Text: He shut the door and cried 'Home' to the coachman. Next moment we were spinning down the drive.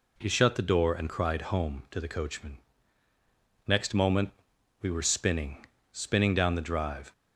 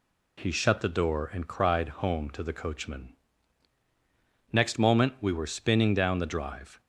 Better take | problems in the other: second | pauses between "moment" and "we"; noticeable; at 4.3 s; 0.48 s long // says "spinning" twice; at 5.9 s

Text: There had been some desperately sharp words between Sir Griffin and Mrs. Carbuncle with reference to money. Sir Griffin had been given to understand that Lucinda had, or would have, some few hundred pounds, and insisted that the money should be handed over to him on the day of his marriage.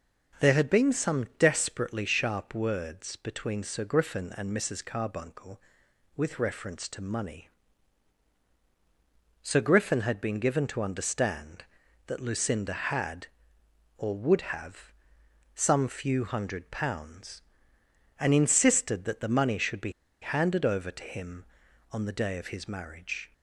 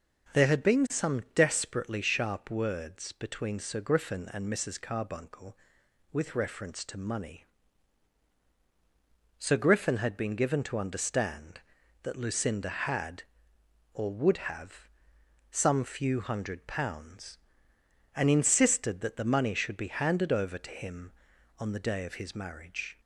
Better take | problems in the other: second | starts louder than the rest; until 1.5 s; 6.5 dB; also in the second // pauses between "be" and "handed"; slight; at 19.9 s; 0.29 s long

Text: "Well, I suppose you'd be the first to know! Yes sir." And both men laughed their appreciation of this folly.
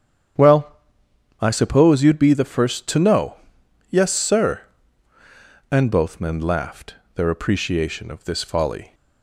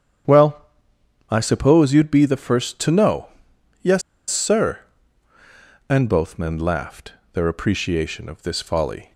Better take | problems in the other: first | starts louder than the rest; strong; until 1.9 s; 8.5 dB; strong in the first // pauses between "Yes" and "sir"; slight; at 4.0 s; 0.28 s long // pauses between "laughed" and "their"; slight; at 7.1 s; 0.18 s long; slight in the first

